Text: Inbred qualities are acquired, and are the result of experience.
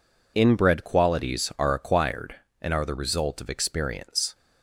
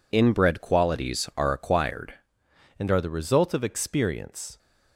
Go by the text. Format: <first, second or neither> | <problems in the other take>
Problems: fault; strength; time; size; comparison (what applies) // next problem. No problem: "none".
first | changes voice at "and"; from 2.7 s on; 1.8 s long